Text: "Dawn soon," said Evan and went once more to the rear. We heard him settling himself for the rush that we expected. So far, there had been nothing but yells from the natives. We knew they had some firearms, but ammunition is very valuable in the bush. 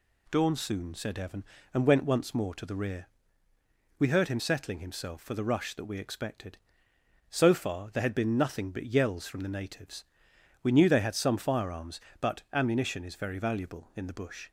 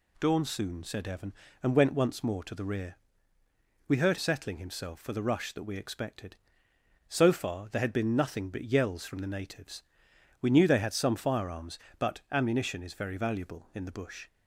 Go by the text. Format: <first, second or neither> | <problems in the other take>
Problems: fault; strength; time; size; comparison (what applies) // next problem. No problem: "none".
first | skips "him"; at 4.1 s